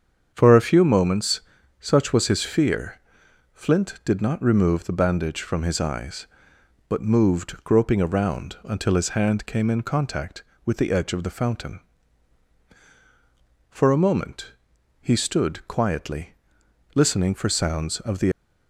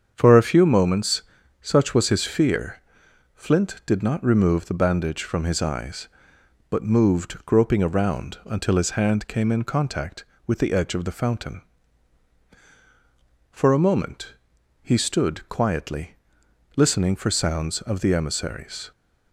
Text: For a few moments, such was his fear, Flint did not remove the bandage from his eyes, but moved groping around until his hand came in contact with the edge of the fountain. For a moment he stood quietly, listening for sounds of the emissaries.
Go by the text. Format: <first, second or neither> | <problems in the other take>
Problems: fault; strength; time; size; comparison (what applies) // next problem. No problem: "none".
second | starts louder than the rest; strong; until 1.3 s; 7.5 dB; strong in the second // pauses between "moment" and "he"; noticeable; at 14.5 s; 0.46 s long; noticeable in the second // stops before "emissaries"; at 18.3 s